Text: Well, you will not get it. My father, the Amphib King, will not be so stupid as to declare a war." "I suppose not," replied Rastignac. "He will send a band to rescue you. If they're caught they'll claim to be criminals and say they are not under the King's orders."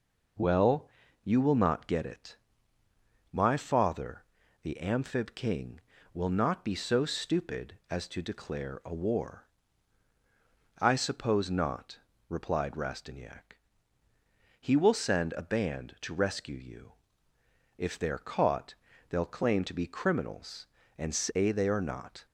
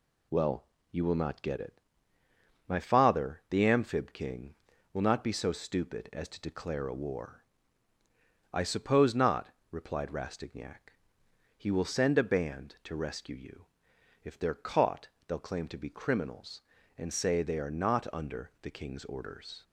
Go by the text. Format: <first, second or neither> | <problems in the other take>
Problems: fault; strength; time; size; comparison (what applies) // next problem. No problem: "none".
second | pauses between "caught" and "they'll"; slight; at 18.7 s; 0.34 s long; slight in the second // stops before "under the King's orders"; at 22.2 s